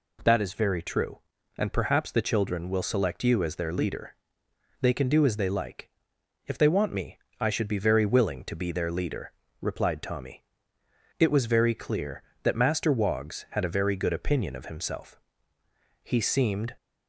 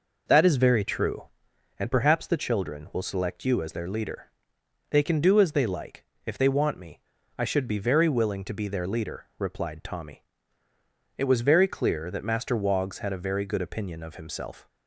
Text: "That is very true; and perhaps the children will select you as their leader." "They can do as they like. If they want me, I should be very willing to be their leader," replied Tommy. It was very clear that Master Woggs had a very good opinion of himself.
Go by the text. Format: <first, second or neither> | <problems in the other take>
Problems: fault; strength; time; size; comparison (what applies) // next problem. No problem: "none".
second | goes on to say "He seemed"; noticeable; from 16.0 s on; 0.72 s long